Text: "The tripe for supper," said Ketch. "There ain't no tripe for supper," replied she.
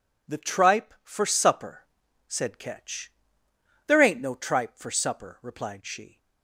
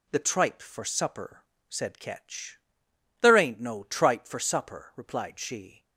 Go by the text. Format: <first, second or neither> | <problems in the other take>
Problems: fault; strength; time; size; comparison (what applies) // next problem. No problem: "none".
neither | none